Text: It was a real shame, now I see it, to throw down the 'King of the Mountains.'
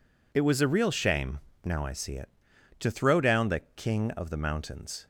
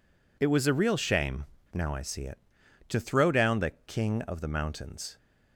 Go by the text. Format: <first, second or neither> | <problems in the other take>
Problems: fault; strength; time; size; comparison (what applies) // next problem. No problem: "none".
neither | none